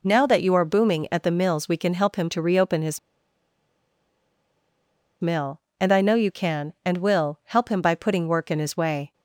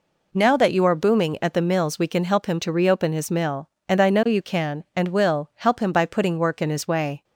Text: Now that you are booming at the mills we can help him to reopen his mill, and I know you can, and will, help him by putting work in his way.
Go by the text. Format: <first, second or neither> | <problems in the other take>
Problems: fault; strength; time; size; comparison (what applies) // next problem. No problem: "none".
second | pauses between "his" and "mill"; strong; at 2.9 s; 2.2 s long